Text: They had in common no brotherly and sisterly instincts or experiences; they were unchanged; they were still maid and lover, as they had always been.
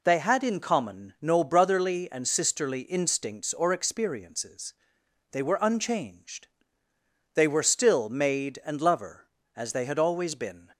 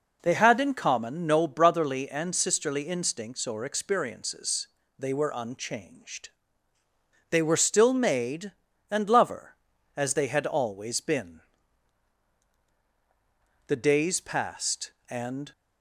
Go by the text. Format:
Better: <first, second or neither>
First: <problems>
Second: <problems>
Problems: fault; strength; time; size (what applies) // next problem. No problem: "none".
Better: first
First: none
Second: goes on to say "The days passed and"; strong; from 13.6 s on; 1.8 s long